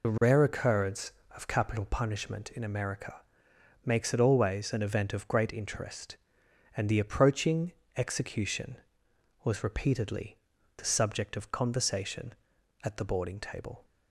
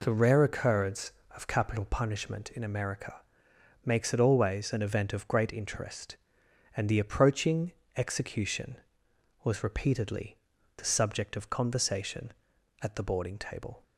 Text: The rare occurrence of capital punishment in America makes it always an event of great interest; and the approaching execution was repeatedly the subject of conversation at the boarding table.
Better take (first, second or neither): second